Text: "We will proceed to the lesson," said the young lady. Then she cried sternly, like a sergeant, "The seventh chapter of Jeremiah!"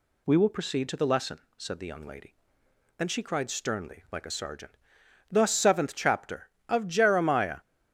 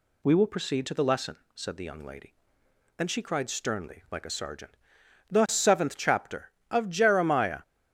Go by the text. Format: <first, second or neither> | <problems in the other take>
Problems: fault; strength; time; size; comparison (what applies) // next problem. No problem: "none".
neither | none